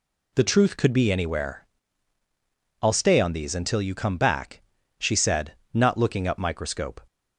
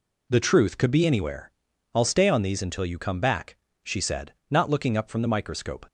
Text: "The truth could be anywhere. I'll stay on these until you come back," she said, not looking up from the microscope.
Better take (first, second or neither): second